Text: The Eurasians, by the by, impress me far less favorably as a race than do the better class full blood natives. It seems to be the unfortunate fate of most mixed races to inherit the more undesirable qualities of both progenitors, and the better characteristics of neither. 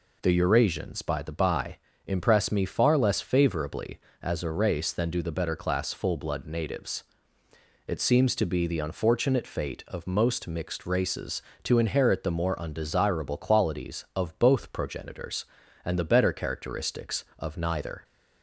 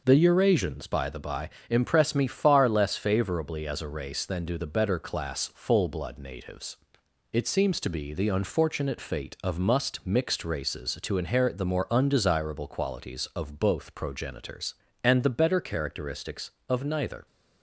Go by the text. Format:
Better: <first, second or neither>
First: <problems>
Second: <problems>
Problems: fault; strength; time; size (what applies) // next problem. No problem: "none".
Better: first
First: none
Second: says "must" for "most"; at 9.5 s